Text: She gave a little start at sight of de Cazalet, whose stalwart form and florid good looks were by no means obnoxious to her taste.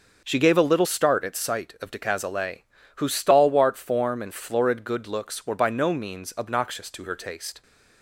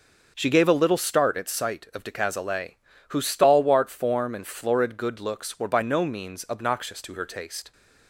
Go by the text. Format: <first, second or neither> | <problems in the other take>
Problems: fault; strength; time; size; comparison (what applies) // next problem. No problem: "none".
neither | starts louder than the rest; the same in both